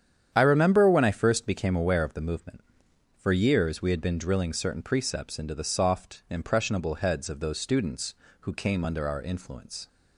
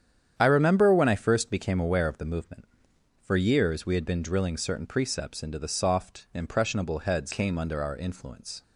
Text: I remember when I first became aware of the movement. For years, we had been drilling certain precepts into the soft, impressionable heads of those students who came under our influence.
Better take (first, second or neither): first